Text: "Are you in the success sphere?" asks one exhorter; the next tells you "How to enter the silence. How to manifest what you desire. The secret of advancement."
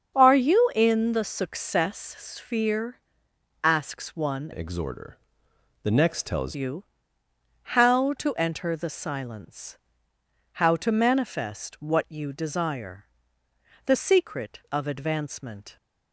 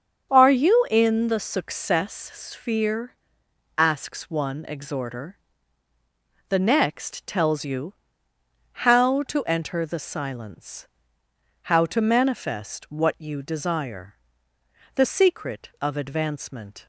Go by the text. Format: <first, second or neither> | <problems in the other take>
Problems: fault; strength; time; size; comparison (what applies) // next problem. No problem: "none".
second | starts louder than the rest; strong; until 1.2 s; 7.5 dB; also in the second // changes voice from "exhorter" to "tells"; from 4.5 to 6.5 s; 2.0 s long // pauses between "you" and "How"; noticeable; at 6.8 s; 0.96 s long; noticeable in the second